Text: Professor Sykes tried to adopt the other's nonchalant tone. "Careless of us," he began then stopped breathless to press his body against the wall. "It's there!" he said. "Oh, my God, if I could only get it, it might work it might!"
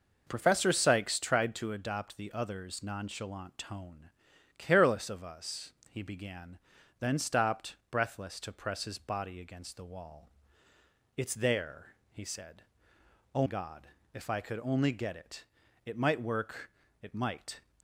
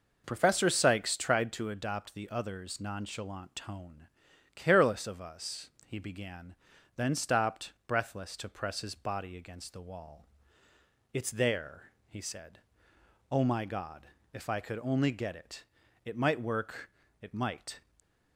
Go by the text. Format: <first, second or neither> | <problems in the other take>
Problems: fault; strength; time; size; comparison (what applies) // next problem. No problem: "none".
second | pauses between "began" and "then"; at 6.5 s; 0.42 s long; also in the second // pauses between "stopped" and "breathless"; slight; at 7.7 s; 0.16 s long; slight in the second // skips "my"; at 13.4 s // pauses between "work" and "it"; slight; at 16.6 s; 0.32 s long; slight in the second